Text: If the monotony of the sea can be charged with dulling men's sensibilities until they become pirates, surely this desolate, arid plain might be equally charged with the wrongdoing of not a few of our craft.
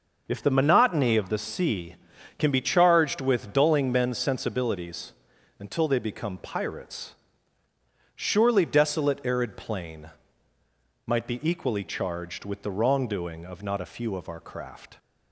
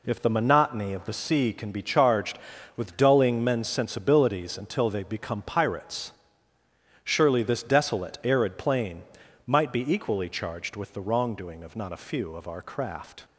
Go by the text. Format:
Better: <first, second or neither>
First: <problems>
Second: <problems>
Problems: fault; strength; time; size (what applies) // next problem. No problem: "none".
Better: second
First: pauses between "sensibilities" and "until"; noticeable; at 5.1 s; 0.46 s long // skips "this"; at 8.6 s // pauses between "plain" and "might"; noticeable; at 10.0 s; 0.96 s long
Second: pauses between "plain" and "might"; at 9.0 s; 0.44 s long